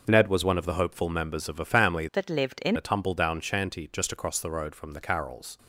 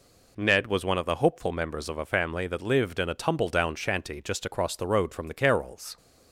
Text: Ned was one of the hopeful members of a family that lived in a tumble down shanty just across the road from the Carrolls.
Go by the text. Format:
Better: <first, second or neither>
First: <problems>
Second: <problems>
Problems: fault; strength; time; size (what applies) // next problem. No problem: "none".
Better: second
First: changes voice from "that" to "in"; from 2.1 to 2.7 s; 0.6 s long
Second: none